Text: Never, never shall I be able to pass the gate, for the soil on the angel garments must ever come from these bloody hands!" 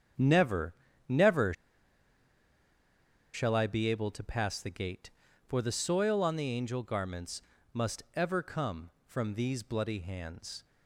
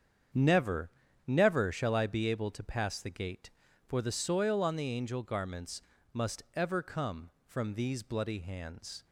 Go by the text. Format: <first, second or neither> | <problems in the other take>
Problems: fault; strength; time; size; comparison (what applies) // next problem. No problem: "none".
second | starts louder than the rest; strong; until 1.5 s; 8 dB; strong in the second // pauses between "never" and "shall"; strong; at 1.5 s; 1.8 s long // pauses between "garments" and "must"; slight; at 7.4 s; 0.32 s long; slight in the second